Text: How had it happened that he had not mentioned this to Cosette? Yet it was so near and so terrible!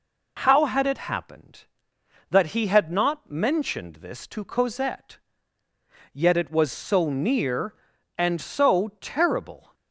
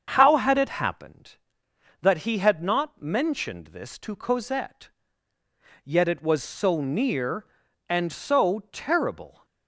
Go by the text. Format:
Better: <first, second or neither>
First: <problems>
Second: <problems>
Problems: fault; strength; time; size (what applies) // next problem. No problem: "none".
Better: first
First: none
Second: starts louder than the rest; until 1.2 s; 7 dB